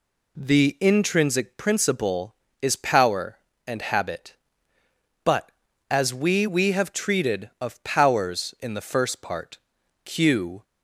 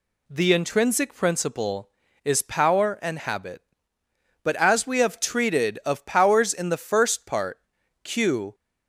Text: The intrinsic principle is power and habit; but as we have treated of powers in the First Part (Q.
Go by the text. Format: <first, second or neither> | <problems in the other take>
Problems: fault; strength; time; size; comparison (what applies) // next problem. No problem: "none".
second | says "we" twice; at 6.4 s